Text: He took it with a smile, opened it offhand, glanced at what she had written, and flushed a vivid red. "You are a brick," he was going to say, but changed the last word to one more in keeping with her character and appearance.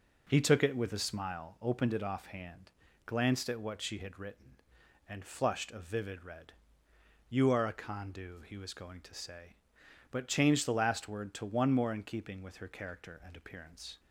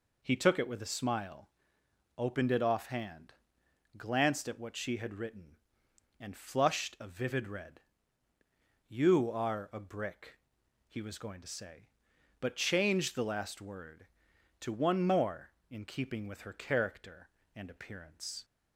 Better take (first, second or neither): second